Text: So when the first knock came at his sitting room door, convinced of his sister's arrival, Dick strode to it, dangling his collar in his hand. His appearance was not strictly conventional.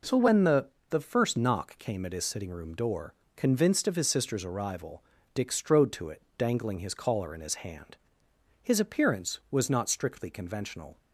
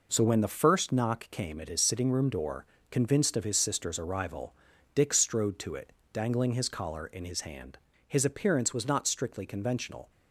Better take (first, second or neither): second